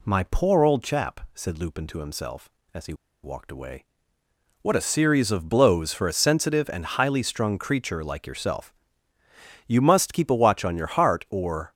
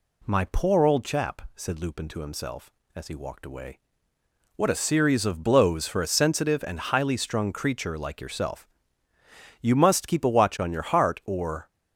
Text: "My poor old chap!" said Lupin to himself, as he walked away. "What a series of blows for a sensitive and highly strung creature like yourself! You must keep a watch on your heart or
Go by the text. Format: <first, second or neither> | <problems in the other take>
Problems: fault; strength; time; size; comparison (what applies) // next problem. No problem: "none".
second | pauses between "he" and "walked"; slight; at 2.9 s; 0.30 s long